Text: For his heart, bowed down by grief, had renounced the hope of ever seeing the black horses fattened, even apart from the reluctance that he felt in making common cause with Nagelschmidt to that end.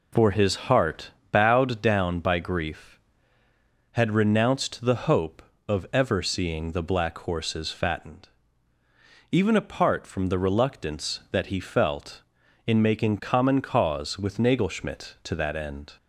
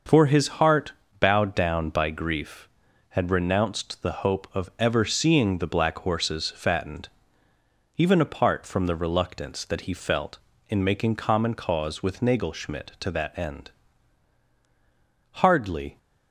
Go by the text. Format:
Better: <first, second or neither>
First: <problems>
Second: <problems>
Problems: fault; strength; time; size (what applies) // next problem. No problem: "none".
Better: first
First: none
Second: starts louder than the rest; noticeable; until 1.4 s; 6 dB // pauses between "his" and "heart"; slight; at 0.4 s; 0.16 s long // goes on to say "Hardly"; from 15.4 s on; 0.56 s long